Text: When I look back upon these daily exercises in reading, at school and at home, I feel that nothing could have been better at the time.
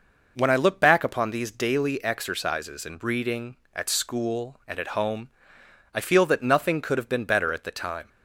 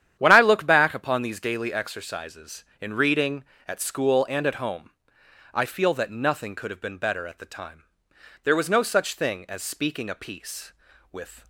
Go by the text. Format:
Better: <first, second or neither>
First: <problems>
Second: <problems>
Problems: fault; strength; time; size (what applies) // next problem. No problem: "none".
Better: first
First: none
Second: starts louder than the rest; strong; until 1.2 s; 10 dB // goes on to say "There was no such thing as speaking a piece with"; strong; from 8.4 s on; 3.0 s long